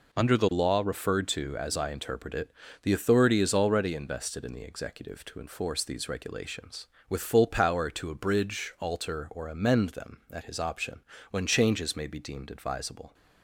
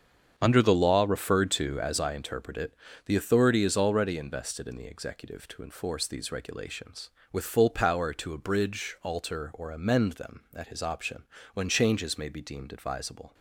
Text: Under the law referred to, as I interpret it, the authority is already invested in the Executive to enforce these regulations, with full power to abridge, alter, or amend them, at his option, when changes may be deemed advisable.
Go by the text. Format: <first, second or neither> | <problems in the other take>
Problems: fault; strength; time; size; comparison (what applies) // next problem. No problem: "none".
first | starts louder than the rest; strong; until 2.2 s; 7.5 dB